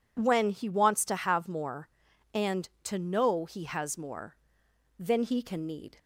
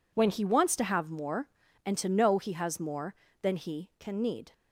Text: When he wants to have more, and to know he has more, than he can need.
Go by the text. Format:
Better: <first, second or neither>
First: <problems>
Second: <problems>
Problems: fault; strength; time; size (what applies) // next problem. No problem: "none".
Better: neither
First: none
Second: none